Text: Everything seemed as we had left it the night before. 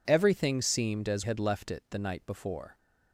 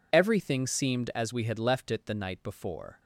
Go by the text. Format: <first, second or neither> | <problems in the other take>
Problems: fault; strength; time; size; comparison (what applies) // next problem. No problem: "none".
second | skips "we"; at 1.2 s